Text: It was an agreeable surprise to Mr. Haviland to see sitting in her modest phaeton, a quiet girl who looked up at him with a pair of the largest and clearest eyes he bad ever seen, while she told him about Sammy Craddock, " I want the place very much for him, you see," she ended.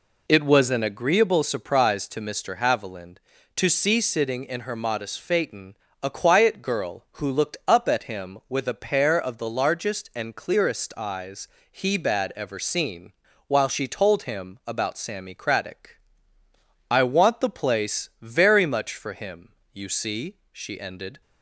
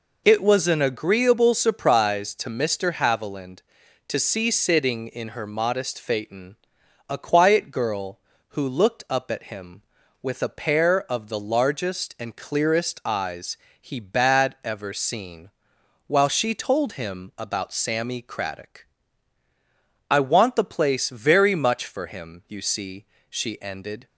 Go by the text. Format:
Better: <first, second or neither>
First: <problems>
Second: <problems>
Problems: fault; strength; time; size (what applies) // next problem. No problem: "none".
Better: neither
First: pauses between "eyes" and "he"; slight; at 11.4 s; 0.24 s long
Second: pauses between "eyes" and "he"; slight; at 13.5 s; 0.20 s long